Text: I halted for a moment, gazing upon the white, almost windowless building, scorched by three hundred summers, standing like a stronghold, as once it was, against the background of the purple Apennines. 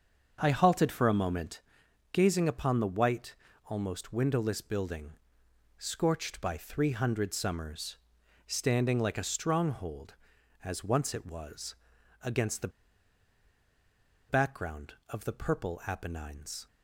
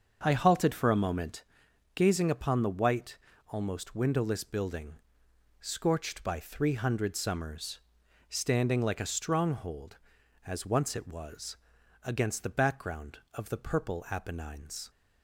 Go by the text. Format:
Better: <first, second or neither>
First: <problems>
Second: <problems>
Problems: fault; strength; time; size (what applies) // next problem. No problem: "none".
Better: second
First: starts louder than the rest; until 1.4 s; 7 dB // pauses between "the" and "background"; strong; at 12.6 s; 1.5 s long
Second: starts louder than the rest; until 1.2 s; 7 dB